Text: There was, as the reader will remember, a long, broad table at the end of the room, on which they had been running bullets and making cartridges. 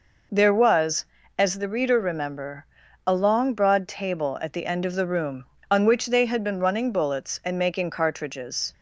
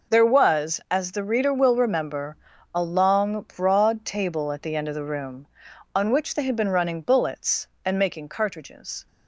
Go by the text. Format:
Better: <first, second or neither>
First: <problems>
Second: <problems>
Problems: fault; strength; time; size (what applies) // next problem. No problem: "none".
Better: second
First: skips "will"; at 1.9 s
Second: none